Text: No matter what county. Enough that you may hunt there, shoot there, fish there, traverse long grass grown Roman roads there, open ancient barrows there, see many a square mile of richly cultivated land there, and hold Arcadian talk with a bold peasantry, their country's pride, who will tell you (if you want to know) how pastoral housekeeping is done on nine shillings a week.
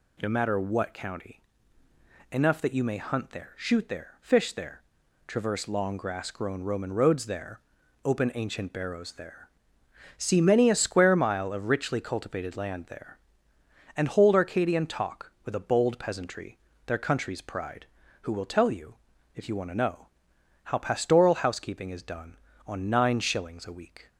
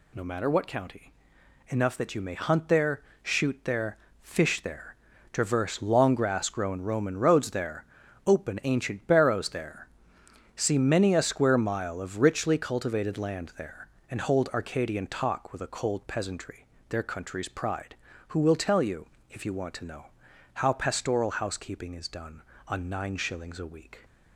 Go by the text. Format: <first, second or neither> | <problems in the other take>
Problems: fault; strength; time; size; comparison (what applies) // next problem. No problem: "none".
first | says "cold" for "bold"; at 15.6 s